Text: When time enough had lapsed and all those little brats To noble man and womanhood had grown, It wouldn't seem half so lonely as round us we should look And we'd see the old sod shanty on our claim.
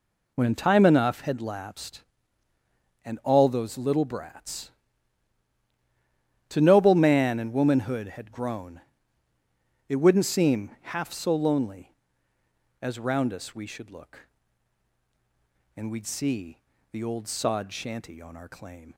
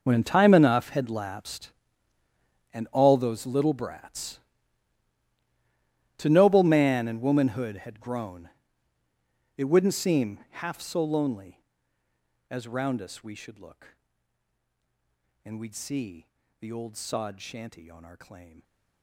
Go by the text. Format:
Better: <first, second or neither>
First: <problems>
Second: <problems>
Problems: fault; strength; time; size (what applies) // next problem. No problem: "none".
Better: first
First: pauses between "see" and "the"; slight; at 16.5 s; 0.32 s long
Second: gets quieter; strong; throughout; 16.5 dB // pauses between "see" and "the"; slight; at 16.2 s; 0.32 s long